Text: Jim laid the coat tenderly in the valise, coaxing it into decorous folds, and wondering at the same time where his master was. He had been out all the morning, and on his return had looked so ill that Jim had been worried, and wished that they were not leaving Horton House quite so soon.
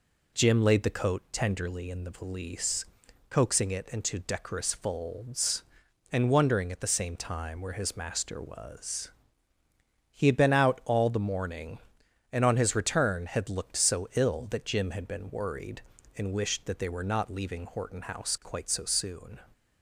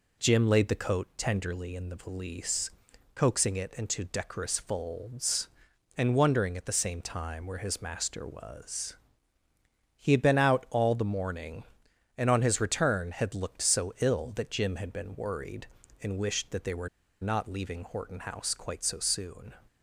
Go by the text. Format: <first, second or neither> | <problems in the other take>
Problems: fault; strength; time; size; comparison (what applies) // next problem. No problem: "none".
first | pauses between "were" and "not"; slight; at 16.8 s; 0.33 s long